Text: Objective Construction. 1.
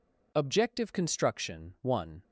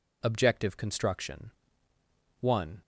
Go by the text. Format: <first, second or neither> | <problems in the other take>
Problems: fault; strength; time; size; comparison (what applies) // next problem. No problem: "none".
neither | none